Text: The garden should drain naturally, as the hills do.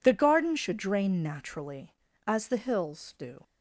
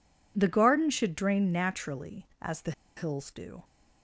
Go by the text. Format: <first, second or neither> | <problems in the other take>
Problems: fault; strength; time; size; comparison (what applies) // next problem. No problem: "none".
first | pauses between "the" and "hills"; slight; at 2.7 s; 0.25 s long